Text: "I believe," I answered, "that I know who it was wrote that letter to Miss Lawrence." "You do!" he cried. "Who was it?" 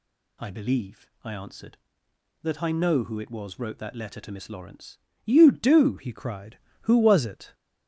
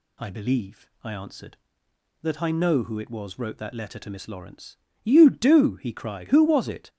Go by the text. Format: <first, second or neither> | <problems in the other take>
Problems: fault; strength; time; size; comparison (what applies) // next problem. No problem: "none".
second | changes voice at "he"; from 5.9 s on; 1.6 s long